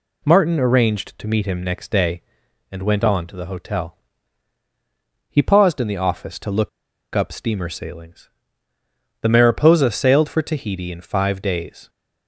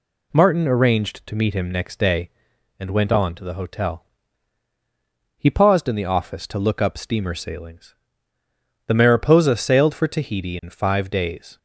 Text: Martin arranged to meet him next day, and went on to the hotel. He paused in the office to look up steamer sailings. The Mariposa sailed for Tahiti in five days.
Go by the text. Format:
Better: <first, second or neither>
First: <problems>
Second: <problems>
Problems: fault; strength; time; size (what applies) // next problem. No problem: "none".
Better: second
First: pauses between "look" and "up"; at 6.6 s; 0.45 s long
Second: none